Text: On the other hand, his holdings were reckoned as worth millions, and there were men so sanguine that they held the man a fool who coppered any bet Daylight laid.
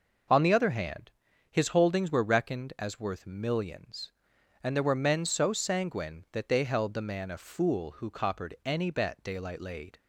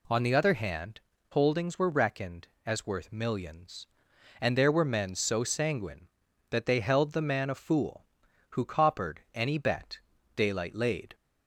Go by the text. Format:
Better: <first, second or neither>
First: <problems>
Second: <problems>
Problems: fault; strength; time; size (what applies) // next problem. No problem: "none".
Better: first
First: none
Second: skips "his"; at 1.1 s // pauses between "bet" and "Daylight"; slight; at 9.9 s; 0.36 s long